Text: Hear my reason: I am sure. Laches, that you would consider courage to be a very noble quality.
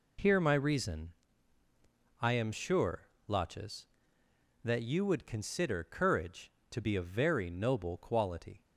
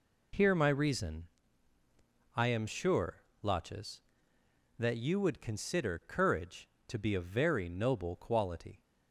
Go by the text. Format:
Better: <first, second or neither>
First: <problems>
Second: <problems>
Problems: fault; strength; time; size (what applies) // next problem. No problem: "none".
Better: neither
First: none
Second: none